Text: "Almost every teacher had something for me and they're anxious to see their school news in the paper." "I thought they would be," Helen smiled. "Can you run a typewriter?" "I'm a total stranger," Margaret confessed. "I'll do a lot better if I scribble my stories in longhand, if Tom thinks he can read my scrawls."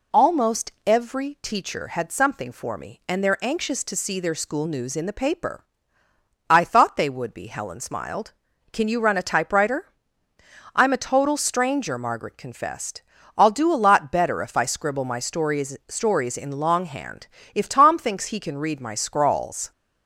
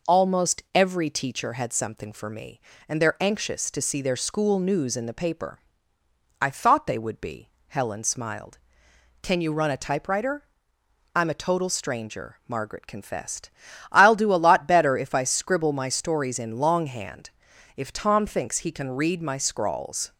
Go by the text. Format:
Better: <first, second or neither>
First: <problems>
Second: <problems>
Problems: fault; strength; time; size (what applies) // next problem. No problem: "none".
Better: second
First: says "stories" twice; at 15.8 s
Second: none